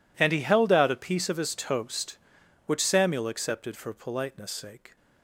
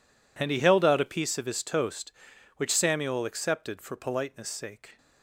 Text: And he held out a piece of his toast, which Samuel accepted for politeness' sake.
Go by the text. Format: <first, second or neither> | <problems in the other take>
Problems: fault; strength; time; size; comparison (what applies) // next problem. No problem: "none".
neither | none